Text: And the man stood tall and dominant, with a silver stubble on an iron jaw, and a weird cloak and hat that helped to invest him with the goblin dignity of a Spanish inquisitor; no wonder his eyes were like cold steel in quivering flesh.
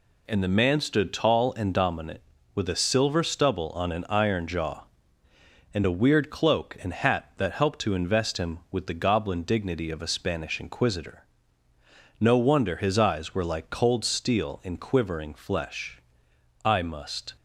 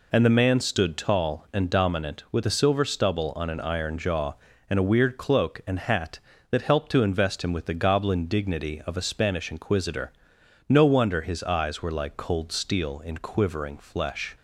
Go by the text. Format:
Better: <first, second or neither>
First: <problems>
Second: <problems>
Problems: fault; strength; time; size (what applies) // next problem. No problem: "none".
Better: second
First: goes on to say "I must"; noticeable; from 16.6 s on; 0.70 s long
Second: none